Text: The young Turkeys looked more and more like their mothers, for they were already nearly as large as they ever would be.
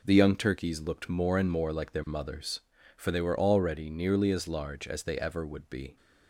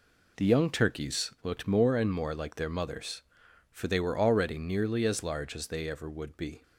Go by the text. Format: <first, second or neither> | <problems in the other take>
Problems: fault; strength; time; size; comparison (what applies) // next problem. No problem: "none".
neither | none